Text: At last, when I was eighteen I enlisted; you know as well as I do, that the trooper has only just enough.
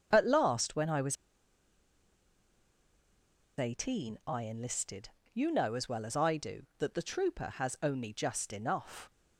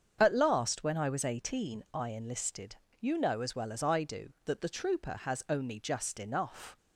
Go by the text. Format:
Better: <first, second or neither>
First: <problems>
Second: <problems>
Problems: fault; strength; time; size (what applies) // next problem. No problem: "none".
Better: second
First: starts louder than the rest; until 1.1 s; 7 dB // pauses between "was" and "eighteen"; strong; at 1.1 s; 2.4 s long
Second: starts louder than the rest; until 1.2 s; 7 dB